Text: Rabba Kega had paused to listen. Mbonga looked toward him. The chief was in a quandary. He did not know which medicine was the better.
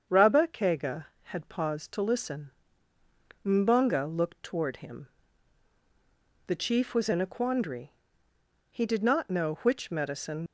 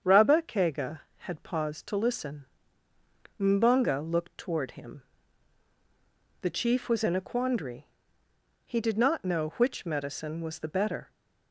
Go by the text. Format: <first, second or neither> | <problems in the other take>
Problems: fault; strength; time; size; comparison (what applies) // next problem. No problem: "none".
second | starts louder than the rest; strong; until 1.2 s; 7.5 dB; strong in the second // stops before "was the better"; at 10.4 s